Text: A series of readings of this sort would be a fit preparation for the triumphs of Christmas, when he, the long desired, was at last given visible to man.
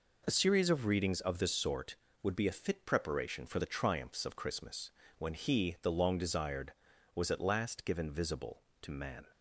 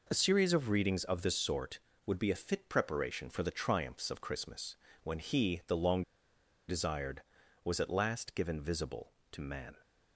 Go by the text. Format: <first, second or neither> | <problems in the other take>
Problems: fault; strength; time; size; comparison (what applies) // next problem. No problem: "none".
first | pauses between "long" and "desired"; noticeable; at 6.0 s; 0.66 s long